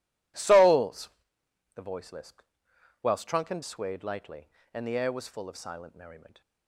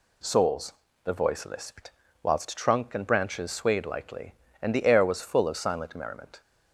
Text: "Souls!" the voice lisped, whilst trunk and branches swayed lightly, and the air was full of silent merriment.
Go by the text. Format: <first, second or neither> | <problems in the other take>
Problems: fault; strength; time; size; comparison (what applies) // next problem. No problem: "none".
second | skips "branches"; at 3.6 s